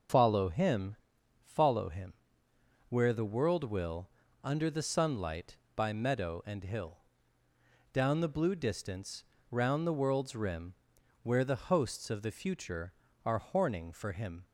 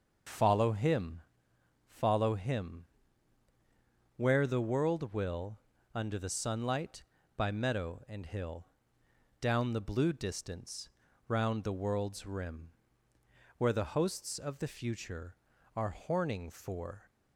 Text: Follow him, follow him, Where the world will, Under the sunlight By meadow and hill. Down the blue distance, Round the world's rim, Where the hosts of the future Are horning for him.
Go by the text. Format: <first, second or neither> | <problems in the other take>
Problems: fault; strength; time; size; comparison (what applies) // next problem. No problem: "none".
first | stops before "him"; at 17.0 s